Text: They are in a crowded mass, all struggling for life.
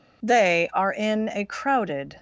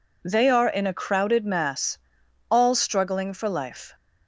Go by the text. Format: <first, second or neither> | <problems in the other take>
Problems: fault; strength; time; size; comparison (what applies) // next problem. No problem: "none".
second | stops before "mass all struggling for life"; at 2.1 s